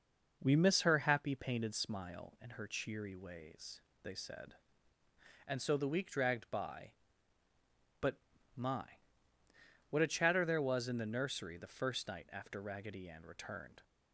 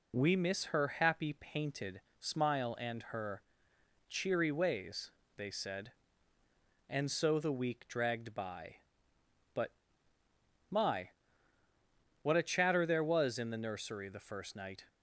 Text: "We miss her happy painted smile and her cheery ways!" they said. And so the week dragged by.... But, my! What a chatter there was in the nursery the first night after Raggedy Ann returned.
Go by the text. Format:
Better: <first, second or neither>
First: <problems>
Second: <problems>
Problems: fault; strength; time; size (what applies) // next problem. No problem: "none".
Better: first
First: none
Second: pauses between "painted" and "smile"; slight; at 1.9 s; 0.22 s long // pauses between "her" and "cheery"; noticeable; at 3.4 s; 0.66 s long // stops before "after Raggedy Ann returned"; at 14.8 s